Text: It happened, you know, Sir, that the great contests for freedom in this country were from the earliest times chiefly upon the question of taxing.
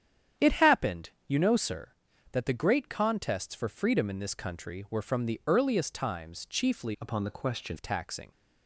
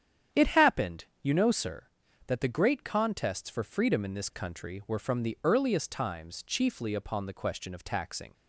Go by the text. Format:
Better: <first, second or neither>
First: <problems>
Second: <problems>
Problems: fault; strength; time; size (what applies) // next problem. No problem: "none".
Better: second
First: starts louder than the rest; strong; until 1.5 s; 9 dB // changes voice from "upon" to "question"; from 7.0 to 7.7 s; 0.7 s long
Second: starts louder than the rest; strong; until 1.5 s; 9 dB